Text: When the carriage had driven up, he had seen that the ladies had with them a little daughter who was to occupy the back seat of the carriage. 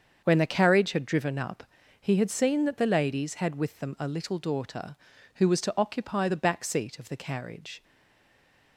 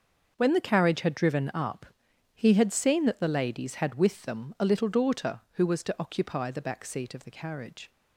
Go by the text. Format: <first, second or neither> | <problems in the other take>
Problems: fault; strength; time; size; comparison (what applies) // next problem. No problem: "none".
second | starts louder than the rest; until 1.2 s; 7 dB; also in the second // stays silent after the last word; from 7.8 s on; 0.9 s long